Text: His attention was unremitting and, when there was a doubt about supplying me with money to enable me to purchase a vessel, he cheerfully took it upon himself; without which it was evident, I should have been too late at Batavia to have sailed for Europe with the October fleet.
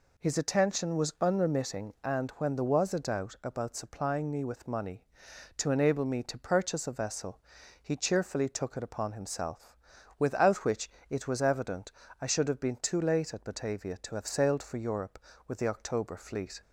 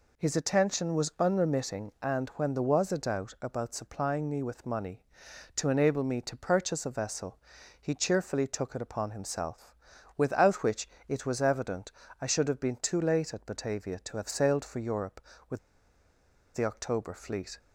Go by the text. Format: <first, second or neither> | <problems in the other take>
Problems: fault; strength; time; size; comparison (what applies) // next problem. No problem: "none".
first | pauses between "which" and "it"; slight; at 10.8 s; 0.22 s long; slight in the first // pauses between "with" and "the"; noticeable; at 15.5 s; 0.95 s long